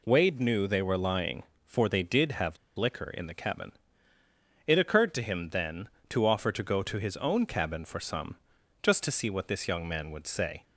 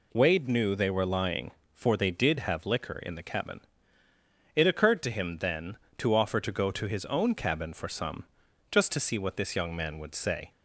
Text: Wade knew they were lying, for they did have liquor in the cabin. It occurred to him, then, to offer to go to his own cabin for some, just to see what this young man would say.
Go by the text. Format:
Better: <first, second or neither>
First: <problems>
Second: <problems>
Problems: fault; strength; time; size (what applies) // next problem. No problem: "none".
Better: second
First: pauses between "have" and "liquor"; slight; at 2.5 s; 0.20 s long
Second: none